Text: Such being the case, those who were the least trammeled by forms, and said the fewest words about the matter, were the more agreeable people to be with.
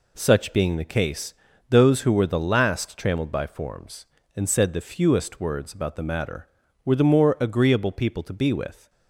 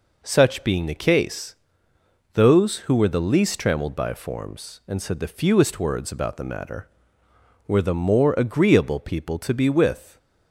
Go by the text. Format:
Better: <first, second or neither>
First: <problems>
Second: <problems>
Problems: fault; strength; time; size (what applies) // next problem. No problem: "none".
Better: second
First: says "last" for "least"; at 2.3 s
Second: none